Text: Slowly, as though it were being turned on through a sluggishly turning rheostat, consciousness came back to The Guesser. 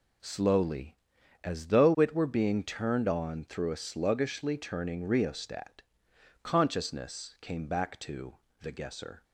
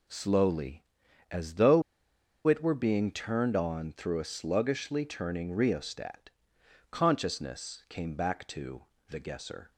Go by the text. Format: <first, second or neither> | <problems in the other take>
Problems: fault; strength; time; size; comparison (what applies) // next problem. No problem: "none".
first | pauses between "though" and "it"; noticeable; at 1.8 s; 0.64 s long // pauses between "to" and "The"; slight; at 8.8 s; 0.24 s long; slight in the first